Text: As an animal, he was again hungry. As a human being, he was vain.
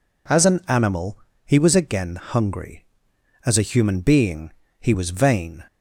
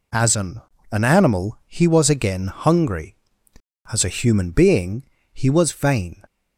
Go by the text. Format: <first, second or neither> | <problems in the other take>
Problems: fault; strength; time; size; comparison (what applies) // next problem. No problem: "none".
first | says "an" twice; at 0.9 s